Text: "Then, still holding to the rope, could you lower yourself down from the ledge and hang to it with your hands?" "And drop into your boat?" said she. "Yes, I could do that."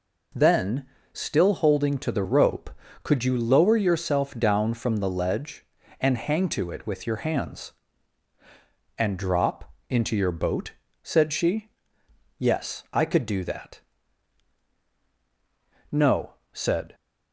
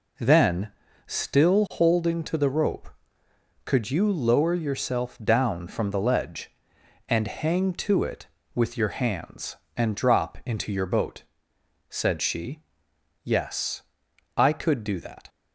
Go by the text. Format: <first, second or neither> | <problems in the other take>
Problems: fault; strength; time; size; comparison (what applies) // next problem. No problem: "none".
second | pauses between "drop" and "into"; slight; at 9.7 s; 0.18 s long // goes on to say "No said"; noticeable; from 15.9 s on; 1.0 s long